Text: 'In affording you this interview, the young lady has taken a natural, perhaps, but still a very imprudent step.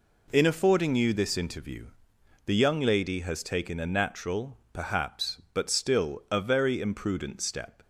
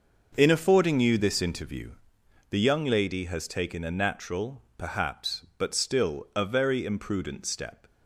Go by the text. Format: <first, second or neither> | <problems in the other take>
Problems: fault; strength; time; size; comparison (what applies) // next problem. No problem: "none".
first | starts louder than the rest; noticeable; until 2.1 s; 6 dB